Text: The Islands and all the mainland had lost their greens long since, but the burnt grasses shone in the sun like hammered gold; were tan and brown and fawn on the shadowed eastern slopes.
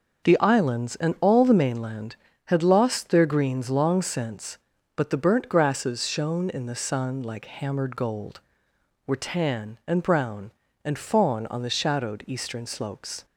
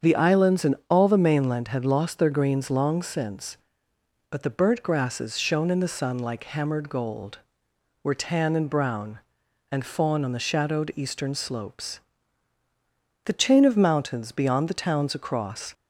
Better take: first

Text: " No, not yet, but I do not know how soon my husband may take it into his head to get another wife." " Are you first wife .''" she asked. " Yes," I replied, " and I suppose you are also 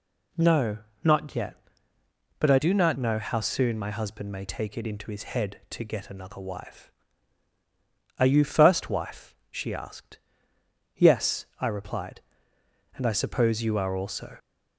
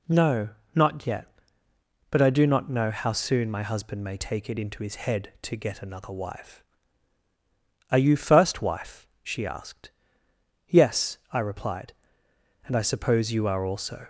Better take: second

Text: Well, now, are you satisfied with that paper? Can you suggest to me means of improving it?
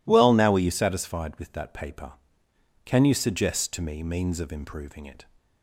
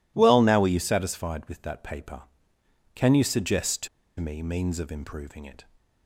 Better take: first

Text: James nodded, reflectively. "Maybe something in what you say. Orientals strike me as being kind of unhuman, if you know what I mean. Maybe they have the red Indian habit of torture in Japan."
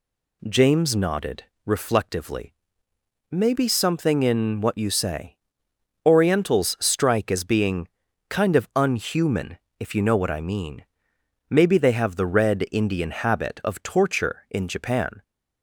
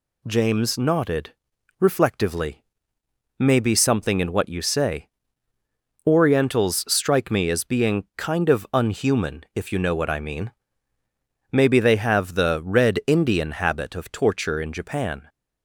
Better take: second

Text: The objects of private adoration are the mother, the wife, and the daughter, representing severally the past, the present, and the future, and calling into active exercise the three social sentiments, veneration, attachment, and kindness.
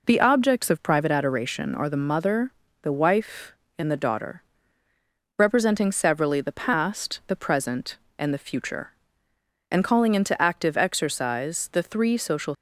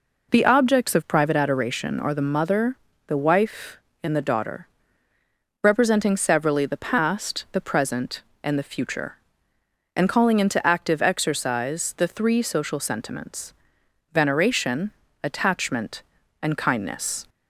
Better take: second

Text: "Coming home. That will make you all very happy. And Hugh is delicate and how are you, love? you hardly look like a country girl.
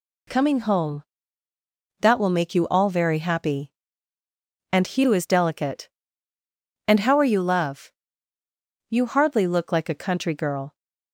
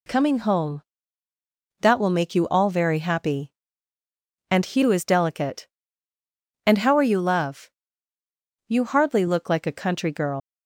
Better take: first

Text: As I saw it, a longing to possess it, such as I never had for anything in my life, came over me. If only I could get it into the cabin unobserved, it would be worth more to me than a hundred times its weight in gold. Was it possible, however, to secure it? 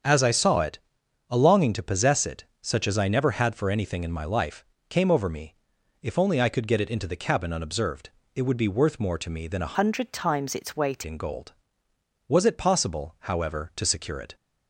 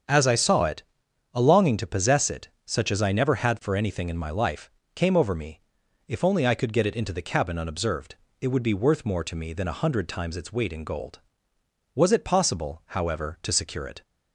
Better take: second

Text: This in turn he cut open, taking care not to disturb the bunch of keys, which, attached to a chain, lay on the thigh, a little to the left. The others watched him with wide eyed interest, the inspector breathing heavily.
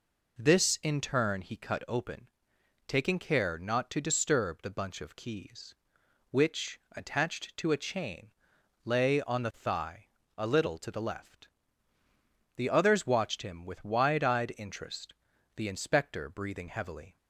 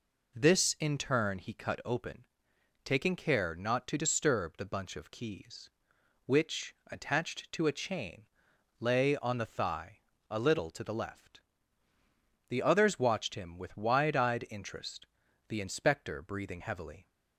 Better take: neither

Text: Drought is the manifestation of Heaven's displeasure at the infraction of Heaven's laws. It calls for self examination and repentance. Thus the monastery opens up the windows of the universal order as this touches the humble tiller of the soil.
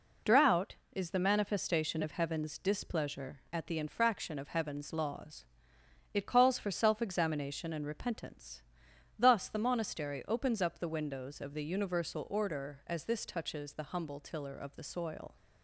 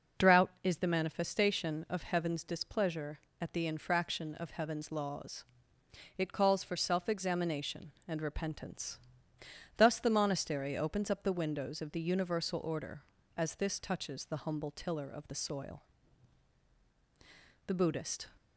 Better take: first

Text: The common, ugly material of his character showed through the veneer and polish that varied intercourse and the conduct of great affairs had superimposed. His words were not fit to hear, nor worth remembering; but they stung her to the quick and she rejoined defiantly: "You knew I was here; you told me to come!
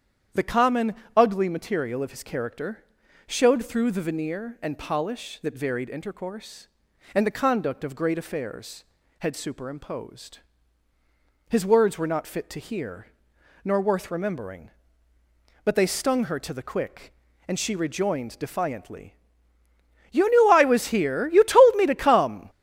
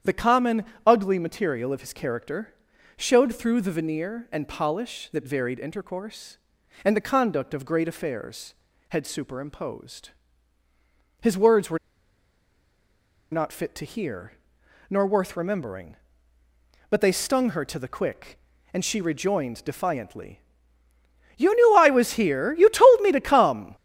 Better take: first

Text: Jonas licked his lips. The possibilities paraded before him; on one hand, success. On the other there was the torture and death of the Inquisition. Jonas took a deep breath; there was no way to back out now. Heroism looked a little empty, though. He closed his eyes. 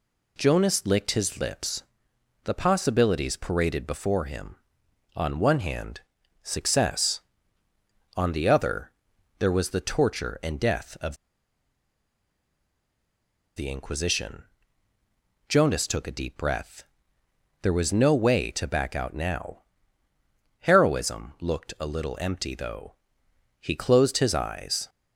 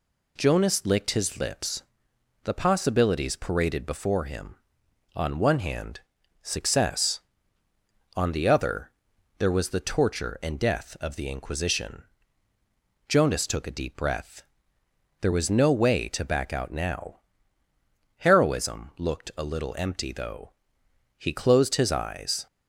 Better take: second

